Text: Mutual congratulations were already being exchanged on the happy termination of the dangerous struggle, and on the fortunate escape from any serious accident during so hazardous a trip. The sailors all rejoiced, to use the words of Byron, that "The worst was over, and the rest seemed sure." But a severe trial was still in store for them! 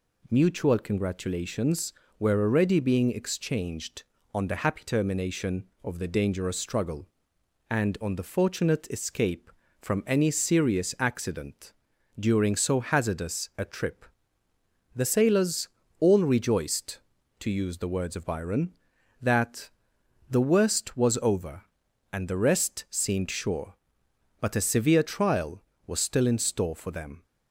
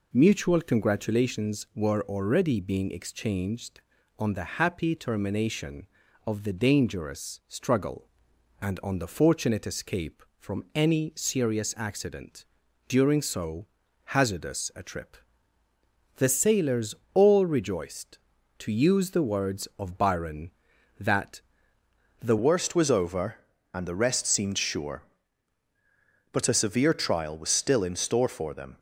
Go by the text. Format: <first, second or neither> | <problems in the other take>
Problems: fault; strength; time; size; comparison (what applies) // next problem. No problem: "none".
first | pauses between "accident" and "during"; at 12.4 s; 0.44 s long; noticeable in the first // pauses between "so" and "hazardous"; at 13.6 s; 0.42 s long // pauses between "sailors" and "all"; slight; at 16.9 s; 0.20 s long; slight in the first // pauses between "that" and "The"; noticeable; at 21.4 s; 0.80 s long; noticeable in the first // changes voice at "worst"; from 22.3 s on; 6.4 s long